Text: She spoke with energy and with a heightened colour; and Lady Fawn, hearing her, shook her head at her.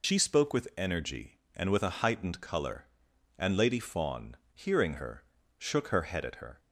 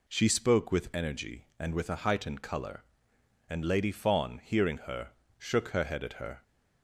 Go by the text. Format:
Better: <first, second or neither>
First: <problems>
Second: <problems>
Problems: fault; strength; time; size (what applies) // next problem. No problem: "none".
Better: second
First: loses the start of "She"; at 0.0 s; 45 ms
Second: none